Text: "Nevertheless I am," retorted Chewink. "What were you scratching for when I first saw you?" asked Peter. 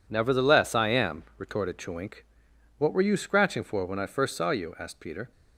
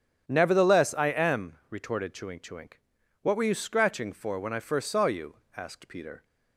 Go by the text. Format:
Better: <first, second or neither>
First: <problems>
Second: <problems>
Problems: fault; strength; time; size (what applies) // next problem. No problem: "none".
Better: first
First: none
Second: starts louder than the rest; until 1.2 s; 7 dB // says "Chewink" twice; at 2.3 s